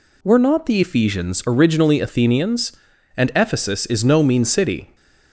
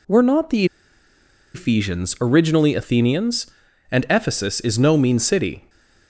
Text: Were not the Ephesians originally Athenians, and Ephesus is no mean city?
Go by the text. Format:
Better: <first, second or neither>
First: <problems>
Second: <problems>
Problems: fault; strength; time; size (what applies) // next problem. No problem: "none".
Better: first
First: none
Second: pauses between "the" and "Ephesians"; noticeable; at 0.6 s; 0.89 s long